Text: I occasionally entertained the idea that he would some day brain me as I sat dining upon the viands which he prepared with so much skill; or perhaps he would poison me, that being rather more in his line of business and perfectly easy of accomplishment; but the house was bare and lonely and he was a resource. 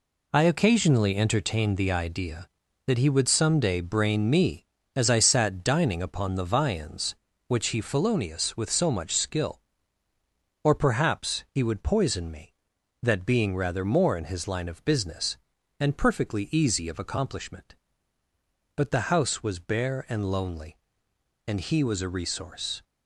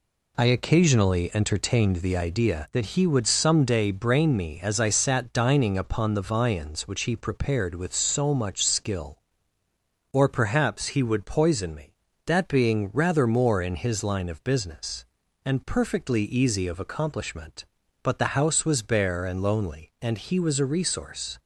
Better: second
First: says "felonious" for "prepared"; at 7.8 s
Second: none

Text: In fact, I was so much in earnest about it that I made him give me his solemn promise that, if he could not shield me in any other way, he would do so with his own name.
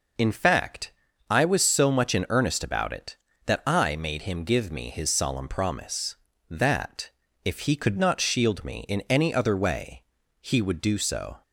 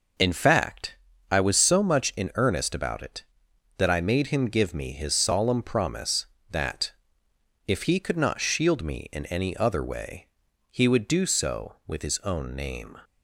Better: second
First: stops before "with his own name"; at 11.4 s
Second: none

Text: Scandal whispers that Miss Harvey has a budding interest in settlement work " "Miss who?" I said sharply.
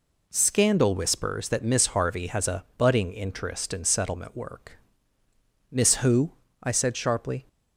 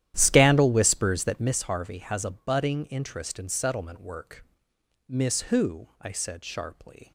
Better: first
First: none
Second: starts louder than the rest; strong; until 1.6 s; 12.5 dB

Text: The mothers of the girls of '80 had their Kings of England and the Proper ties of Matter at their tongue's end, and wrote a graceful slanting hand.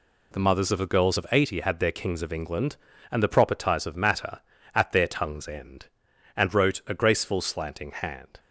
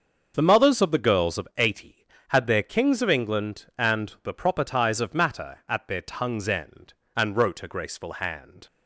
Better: first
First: none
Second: starts louder than the rest; until 1.3 s; 6.5 dB // skips "slanting"; at 8.1 s

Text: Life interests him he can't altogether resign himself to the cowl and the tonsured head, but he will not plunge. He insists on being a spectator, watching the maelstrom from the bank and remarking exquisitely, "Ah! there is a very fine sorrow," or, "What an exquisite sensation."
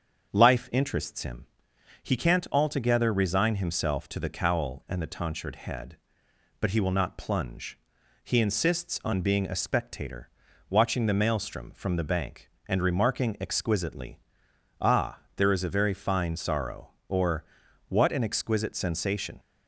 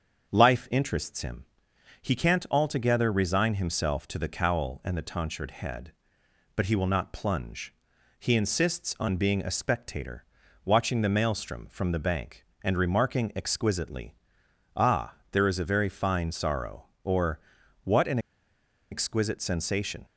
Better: first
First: starts louder than the rest; until 1.3 s; 7 dB // pauses between "him" and "he"; noticeable; at 1.4 s; 0.56 s long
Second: starts louder than the rest; until 1.3 s; 7 dB // pauses between "him" and "he"; noticeable; at 1.4 s; 0.56 s long // pauses between "an" and "exquisite"; noticeable; at 18.1 s; 0.72 s long

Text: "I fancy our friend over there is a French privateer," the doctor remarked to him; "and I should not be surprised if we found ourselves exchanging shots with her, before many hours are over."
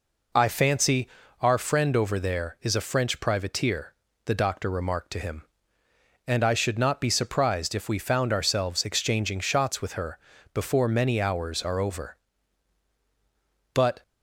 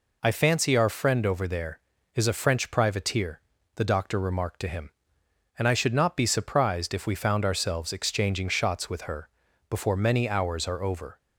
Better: second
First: pauses between "fancy" and "our"; slight; at 1.0 s; 0.32 s long // goes on to say "But"; slight; from 13.7 s on; 0.28 s long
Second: none

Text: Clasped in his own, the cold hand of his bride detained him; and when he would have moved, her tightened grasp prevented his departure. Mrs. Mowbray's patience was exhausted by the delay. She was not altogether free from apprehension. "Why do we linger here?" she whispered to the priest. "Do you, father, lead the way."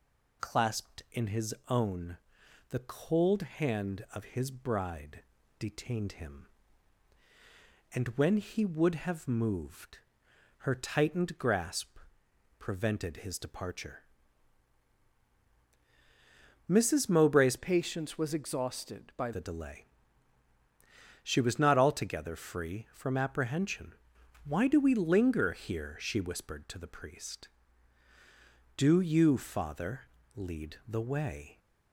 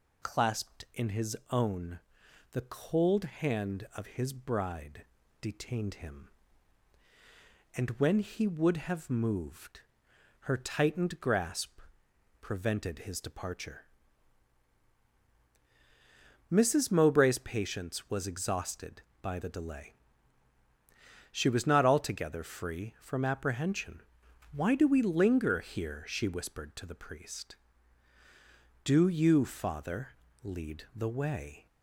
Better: second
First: pauses between "bride" and "detained"; slight; at 5.2 s; 0.36 s long // pauses between "grasp" and "prevented"; noticeable; at 11.9 s; 0.60 s long // changes voice from "patience" to "by"; from 17.5 to 19.3 s; 1.8 s long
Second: pauses between "bride" and "detained"; slight; at 5.0 s; 0.36 s long // pauses between "grasp" and "prevented"; noticeable; at 11.8 s; 0.60 s long

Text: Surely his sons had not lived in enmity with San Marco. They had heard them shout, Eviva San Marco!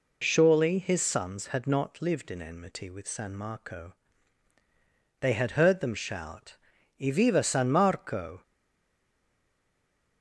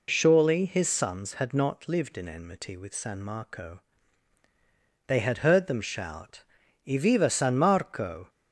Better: second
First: stays silent after the last word; noticeable; from 8.4 s on; 1.8 s long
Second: none

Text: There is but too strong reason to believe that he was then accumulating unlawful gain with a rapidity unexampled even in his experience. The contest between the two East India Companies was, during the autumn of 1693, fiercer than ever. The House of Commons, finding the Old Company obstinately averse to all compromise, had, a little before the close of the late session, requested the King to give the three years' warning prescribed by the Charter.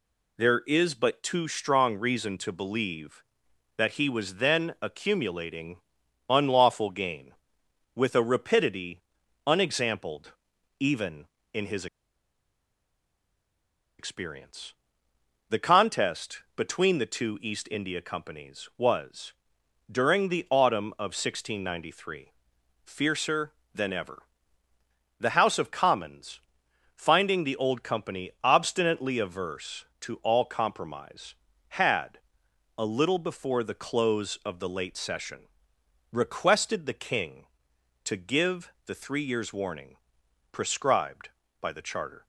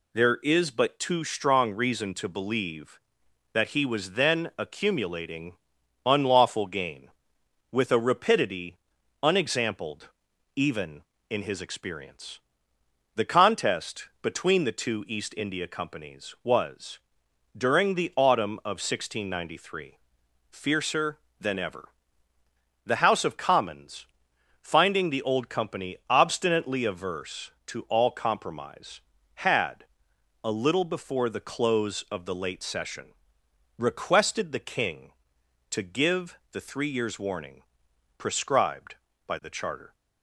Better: second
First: pauses between "accumulating" and "unlawful"; noticeable; at 5.7 s; 0.50 s long // pauses between "rapidity" and "unexampled"; at 9.0 s; 0.44 s long // pauses between "unexampled" and "even"; at 10.3 s; 0.44 s long // pauses between "his" and "experience"; strong; at 11.8 s; 2.1 s long // pauses between "warning" and "prescribed"; noticeable; at 39.9 s; 0.56 s long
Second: pauses between "accumulating" and "unlawful"; noticeable; at 5.5 s; 0.50 s long // pauses between "rapidity" and "unexampled"; at 8.7 s; 0.44 s long // pauses between "unexampled" and "even"; at 10.0 s; 0.44 s long // pauses between "warning" and "prescribed"; noticeable; at 37.6 s; 0.56 s long

